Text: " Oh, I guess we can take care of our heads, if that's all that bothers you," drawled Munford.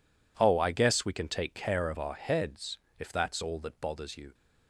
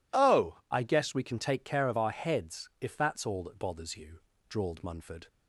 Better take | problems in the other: second | stops before "drawled Munford"; at 4.3 s

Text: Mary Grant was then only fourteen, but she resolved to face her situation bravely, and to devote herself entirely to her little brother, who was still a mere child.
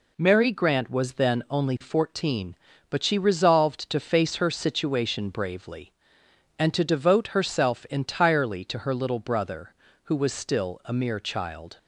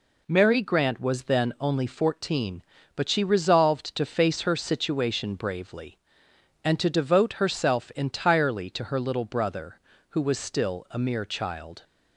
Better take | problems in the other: neither | none

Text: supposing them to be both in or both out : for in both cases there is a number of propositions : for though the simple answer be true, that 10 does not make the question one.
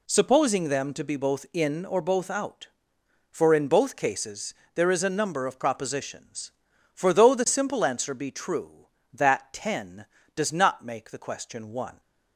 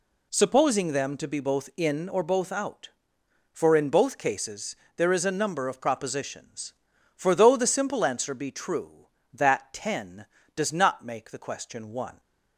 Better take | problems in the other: neither | pauses between "cases" and "there"; slight; the same in both

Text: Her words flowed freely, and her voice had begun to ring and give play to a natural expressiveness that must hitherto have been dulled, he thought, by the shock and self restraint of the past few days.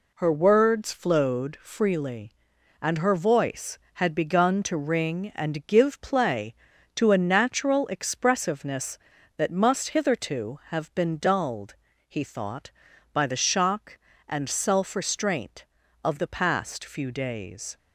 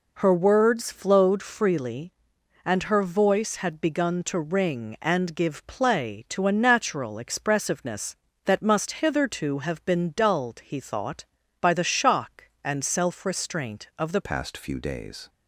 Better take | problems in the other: first | changes voice at "past"; from 14.2 s on; 1.0 s long

